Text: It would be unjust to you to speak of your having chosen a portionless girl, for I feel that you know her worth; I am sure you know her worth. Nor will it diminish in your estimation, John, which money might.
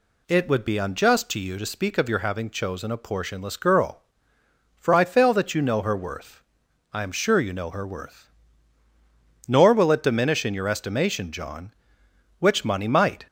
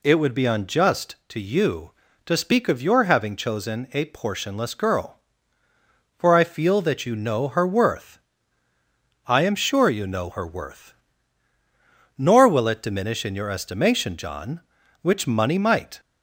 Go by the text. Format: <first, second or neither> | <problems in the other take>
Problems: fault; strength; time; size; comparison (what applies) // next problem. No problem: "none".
second | says "fail" for "feel"; at 5.0 s